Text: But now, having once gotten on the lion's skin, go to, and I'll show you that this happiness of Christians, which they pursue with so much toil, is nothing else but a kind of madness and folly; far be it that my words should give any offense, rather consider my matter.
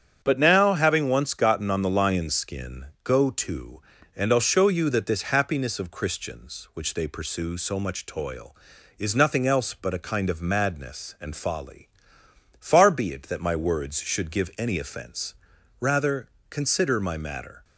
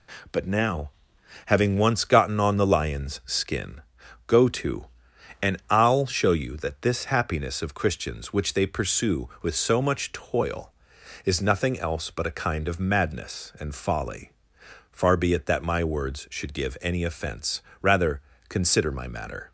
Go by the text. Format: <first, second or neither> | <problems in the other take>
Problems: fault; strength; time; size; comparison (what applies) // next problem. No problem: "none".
second | starts louder than the rest; strong; until 1.2 s; 8 dB // skips "with"; at 7.5 s // pauses between "rather" and "consider"; slight; at 16.2 s; 0.22 s long; slight in the second